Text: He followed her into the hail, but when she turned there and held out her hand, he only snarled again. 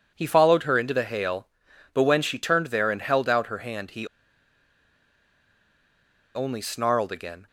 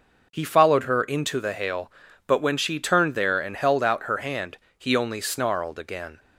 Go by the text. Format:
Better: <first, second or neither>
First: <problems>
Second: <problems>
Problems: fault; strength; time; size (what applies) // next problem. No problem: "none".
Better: second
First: pauses between "he" and "only"; strong; at 4.0 s; 2.2 s long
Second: none